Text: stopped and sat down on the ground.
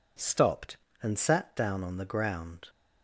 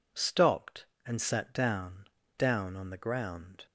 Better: first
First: none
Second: says "down" twice; at 2.3 s

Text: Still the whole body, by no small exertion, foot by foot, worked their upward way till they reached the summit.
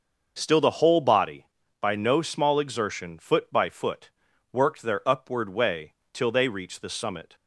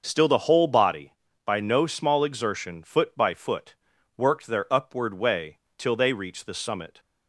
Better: neither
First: starts louder than the rest; noticeable; until 1.3 s; 6 dB // pauses between "way" and "till"; slight; at 5.9 s; 0.18 s long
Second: starts louder than the rest; noticeable; until 1.0 s; 6 dB // pauses between "way" and "till"; slight; at 5.5 s; 0.18 s long

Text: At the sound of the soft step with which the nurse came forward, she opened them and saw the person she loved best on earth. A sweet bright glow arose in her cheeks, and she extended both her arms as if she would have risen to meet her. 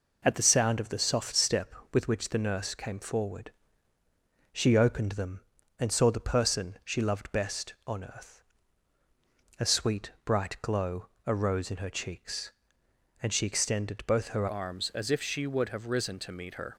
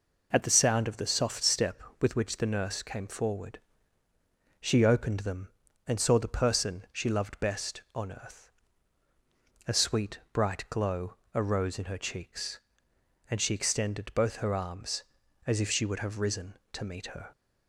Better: second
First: pauses between "glow" and "arose"; slight; at 11.0 s; 0.20 s long // changes voice at "arms"; from 14.4 s on; 2.3 s long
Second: pauses between "glow" and "arose"; slight; at 11.1 s; 0.20 s long

